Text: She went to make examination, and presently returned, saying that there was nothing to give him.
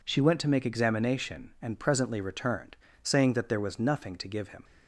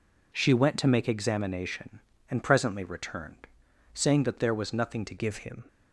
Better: first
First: none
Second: changes voice at "give"; from 5.1 s on; 0.5 s long

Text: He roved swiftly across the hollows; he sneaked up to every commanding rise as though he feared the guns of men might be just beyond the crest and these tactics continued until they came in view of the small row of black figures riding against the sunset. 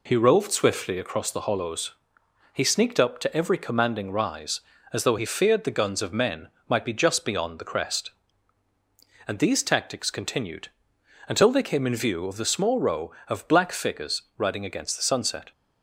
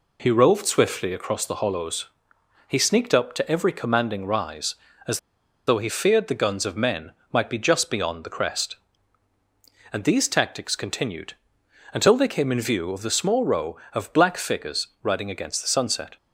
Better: first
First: pauses between "men" and "might"; slight; at 6.4 s; 0.20 s long // pauses between "continued" and "until"; noticeable; at 10.6 s; 0.62 s long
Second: pauses between "as" and "though"; noticeable; at 5.1 s; 0.50 s long // pauses between "men" and "might"; slight; at 7.1 s; 0.20 s long // pauses between "continued" and "until"; noticeable; at 11.3 s; 0.62 s long

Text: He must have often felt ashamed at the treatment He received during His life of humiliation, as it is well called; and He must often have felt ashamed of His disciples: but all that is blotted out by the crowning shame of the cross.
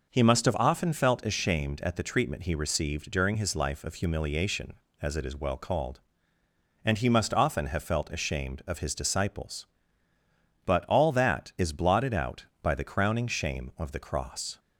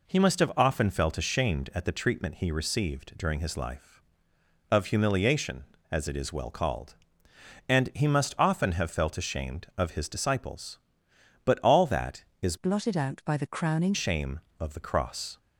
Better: first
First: none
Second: changes voice from "blotted" to "crowning"; from 12.5 to 13.9 s; 1.4 s long

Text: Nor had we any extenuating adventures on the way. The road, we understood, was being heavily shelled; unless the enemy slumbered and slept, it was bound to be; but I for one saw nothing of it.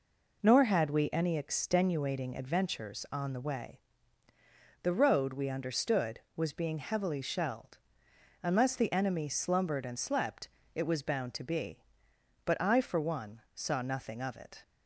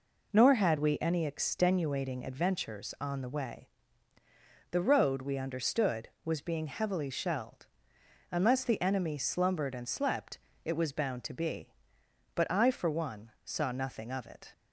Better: neither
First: none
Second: none

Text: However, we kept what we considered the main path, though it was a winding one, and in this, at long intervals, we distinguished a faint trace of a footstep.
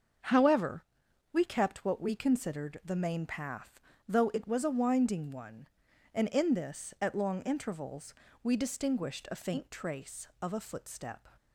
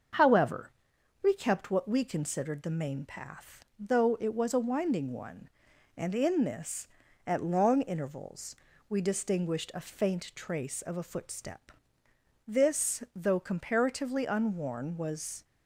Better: first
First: starts louder than the rest; until 1.7 s; 6.5 dB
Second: starts louder than the rest; until 1.6 s; 6.5 dB // goes on to say "This though comparatively unworn was"; strong; from 12.4 s on; 2.9 s long

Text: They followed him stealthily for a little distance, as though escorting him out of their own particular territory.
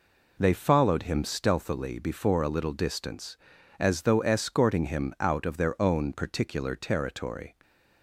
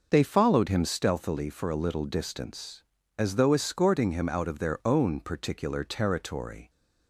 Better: second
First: says "before" for "for"; at 1.9 s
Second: none

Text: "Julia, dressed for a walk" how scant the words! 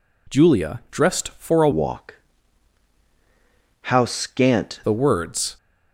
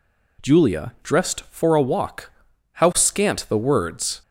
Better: second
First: changes voice from "walk" to "scant"; from 1.7 to 4.7 s; 3.0 s long // pauses between "walk" and "how"; strong; at 2.1 s; 1.6 s long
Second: pauses between "walk" and "how"; at 2.3 s; 0.40 s long

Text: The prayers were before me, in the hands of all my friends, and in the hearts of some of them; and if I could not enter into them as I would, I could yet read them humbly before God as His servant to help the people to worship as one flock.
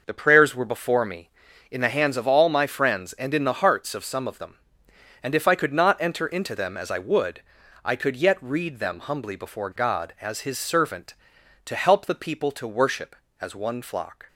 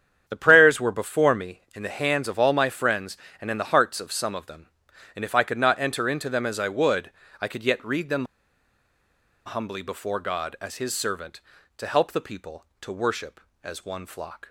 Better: first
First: none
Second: starts louder than the rest; strong; until 1.2 s; 9 dB // pauses between "them" and "humbly"; at 8.2 s; 1.2 s long

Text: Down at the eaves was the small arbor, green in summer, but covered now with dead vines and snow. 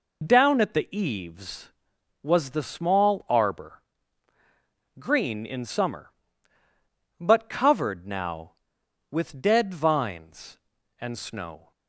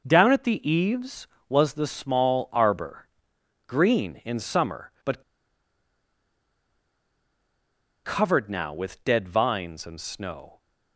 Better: first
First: none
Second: pauses between "but" and "covered"; strong; at 5.2 s; 2.8 s long

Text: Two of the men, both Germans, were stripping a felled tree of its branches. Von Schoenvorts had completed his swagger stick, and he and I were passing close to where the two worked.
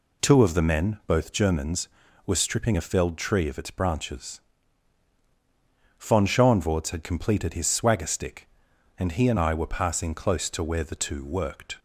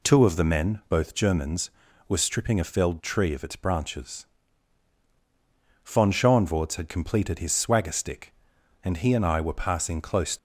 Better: first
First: none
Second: stops before "to where the two worked"; at 10.3 s

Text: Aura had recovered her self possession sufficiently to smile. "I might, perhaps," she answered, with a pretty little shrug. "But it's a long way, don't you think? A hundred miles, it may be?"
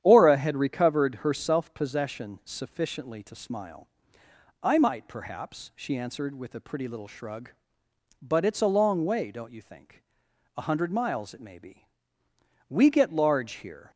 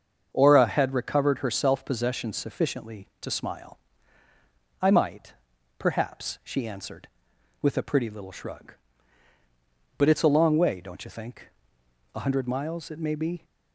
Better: second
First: starts louder than the rest; strong; until 1.0 s; 10 dB // goes on to say "We get large here"; noticeable; from 12.7 s on; 1.2 s long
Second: starts louder than the rest; until 1.3 s; 7 dB

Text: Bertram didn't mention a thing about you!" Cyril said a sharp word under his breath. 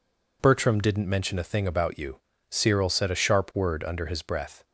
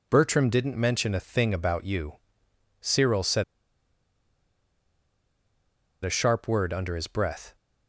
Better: first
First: none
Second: pauses between "said" and "a"; strong; at 3.4 s; 2.6 s long

